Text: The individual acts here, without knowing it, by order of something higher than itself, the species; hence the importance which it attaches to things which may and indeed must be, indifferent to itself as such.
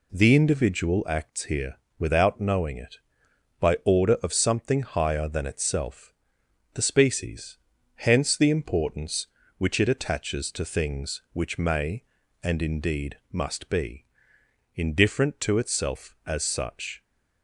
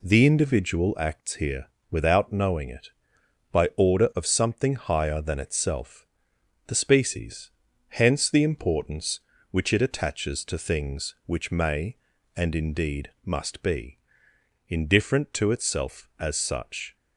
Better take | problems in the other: neither | none

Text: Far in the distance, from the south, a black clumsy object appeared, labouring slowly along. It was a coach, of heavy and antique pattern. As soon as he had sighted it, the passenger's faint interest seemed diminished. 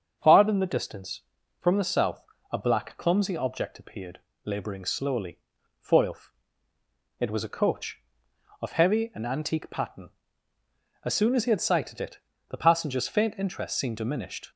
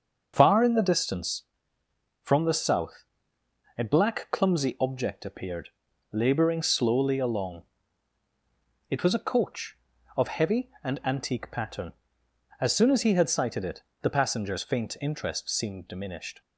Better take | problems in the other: second | starts louder than the rest; until 1.2 s; 7 dB; also in the second // says "foilf" for "along"; at 5.8 s

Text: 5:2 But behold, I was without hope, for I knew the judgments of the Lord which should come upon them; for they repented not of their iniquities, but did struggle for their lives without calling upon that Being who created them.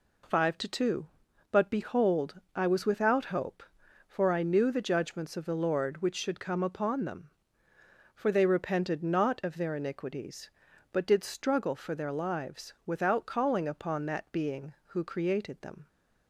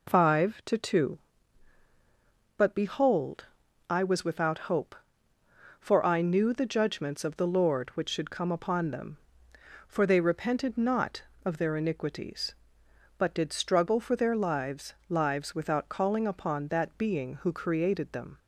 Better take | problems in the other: first | says "lives" twice; at 15.1 s

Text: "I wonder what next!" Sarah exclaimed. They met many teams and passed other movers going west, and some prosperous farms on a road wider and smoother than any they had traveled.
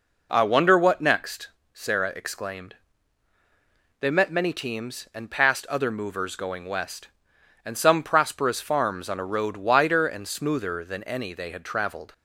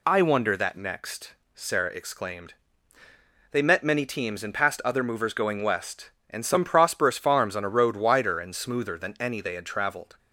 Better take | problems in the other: first | says "that" for "what"; at 0.5 s

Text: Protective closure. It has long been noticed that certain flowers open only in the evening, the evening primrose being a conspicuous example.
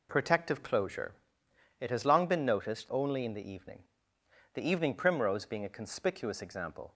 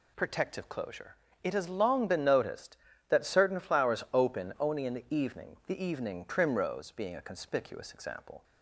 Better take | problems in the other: second | skips "that certain flowers open"; at 2.9 s

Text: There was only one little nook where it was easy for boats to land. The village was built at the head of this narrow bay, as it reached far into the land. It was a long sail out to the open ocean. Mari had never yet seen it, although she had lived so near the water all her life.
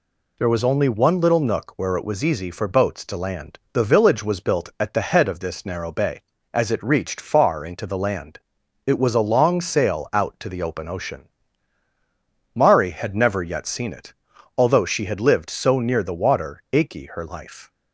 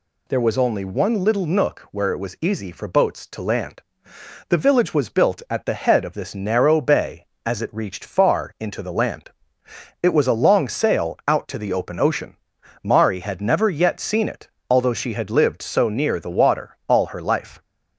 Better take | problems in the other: second | says "achy" for "all"; at 16.7 s

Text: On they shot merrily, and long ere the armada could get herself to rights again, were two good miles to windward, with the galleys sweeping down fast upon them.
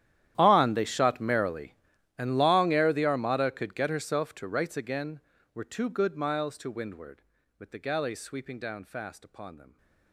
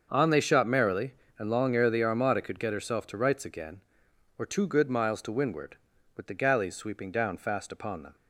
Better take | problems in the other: second | gets quieter; strong; throughout; 23 dB // starts louder than the rest; strong; until 1.3 s; 11.5 dB; also in the second

